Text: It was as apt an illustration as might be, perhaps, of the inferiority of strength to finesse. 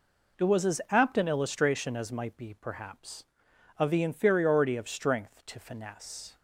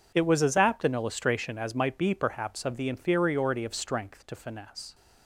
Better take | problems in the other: neither | none

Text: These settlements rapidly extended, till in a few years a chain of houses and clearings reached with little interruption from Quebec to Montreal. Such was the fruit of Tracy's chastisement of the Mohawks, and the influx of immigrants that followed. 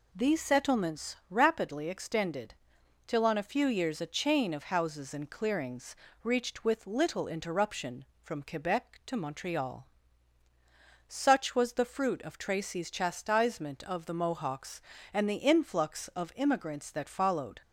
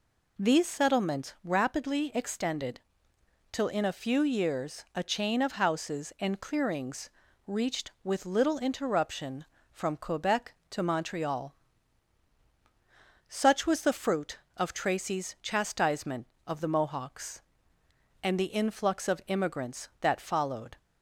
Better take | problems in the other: second | says "on" for "in"; at 3.2 s // pauses between "clearings" and "reached"; slight; at 5.9 s; 0.30 s long; also in the second

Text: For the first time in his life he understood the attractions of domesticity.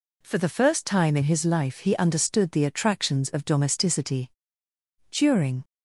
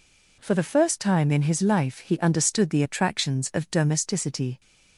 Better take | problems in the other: second | goes on to say "During"; from 5.0 s on; 0.54 s long

